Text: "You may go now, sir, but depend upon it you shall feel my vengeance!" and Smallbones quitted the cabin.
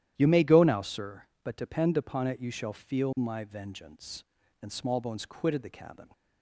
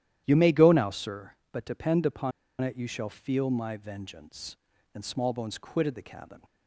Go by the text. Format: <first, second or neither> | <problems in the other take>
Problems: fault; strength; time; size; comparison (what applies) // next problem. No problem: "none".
first | starts louder than the rest; strong; until 1.2 s; 12 dB; strong in the first // pauses between "upon" and "it"; slight; at 2.3 s; 0.30 s long